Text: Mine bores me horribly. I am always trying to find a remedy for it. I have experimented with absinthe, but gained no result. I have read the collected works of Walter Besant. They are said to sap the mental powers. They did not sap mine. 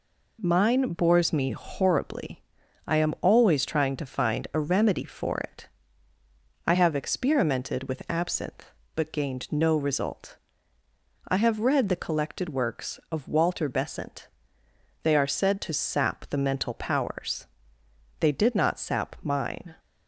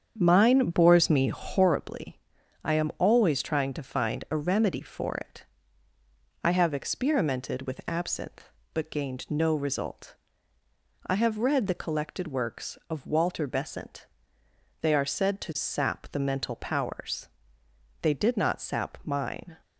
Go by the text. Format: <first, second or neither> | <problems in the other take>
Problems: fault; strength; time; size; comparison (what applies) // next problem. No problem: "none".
first | starts louder than the rest; strong; until 1.8 s; 7.5 dB